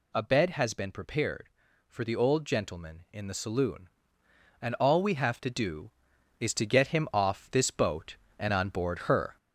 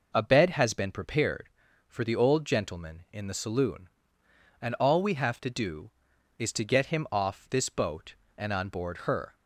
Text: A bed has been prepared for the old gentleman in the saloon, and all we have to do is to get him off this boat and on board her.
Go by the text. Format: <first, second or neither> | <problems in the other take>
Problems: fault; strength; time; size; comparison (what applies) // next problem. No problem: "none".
second | gets louder; noticeable; throughout; 4 dB